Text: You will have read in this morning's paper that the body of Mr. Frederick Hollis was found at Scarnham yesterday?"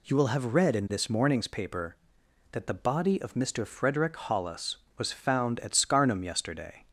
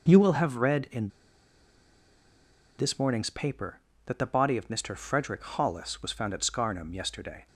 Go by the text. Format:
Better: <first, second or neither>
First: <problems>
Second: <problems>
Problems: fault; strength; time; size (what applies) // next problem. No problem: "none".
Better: first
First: none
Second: pauses between "in" and "this"; strong; at 1.0 s; 1.6 s long